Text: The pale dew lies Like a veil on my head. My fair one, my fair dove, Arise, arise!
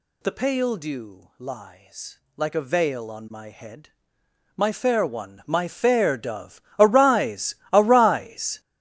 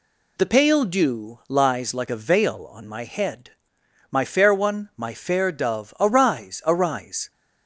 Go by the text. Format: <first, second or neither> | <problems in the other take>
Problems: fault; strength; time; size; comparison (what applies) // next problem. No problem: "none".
second | gets louder; strong; throughout; 12 dB // pauses between "lies" and "Like"; slight; at 2.1 s; 0.18 s long